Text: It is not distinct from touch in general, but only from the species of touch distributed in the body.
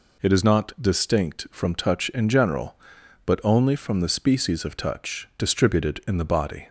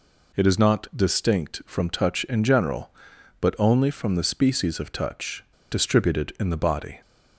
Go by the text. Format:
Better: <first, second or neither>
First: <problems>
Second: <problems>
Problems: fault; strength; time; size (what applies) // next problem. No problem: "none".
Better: first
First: none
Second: pauses between "touch" and "distributed"; slight; at 5.4 s; 0.26 s long